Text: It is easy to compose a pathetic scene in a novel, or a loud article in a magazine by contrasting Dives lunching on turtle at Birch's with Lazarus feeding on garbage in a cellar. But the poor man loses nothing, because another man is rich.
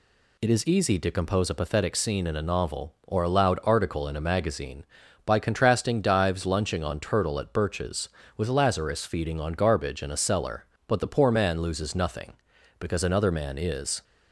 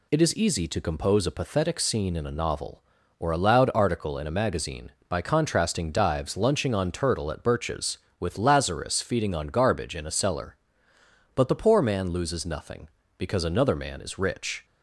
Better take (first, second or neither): second